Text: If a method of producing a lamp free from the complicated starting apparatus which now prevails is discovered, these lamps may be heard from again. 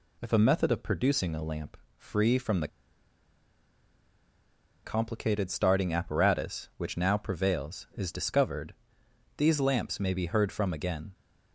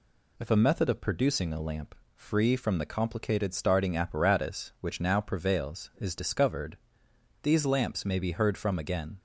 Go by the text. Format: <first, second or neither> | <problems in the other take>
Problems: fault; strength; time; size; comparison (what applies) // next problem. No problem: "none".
second | pauses between "lamp" and "free"; slight; at 1.7 s; 0.20 s long; slight in the second // pauses between "the" and "complicated"; strong; at 2.6 s; 2.1 s long